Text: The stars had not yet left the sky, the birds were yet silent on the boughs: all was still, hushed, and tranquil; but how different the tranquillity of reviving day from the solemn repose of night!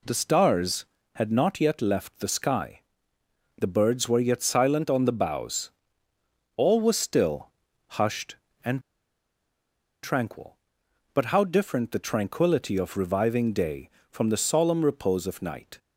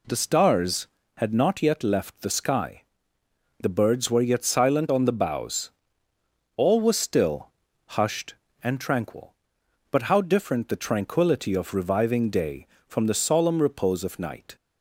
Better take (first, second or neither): second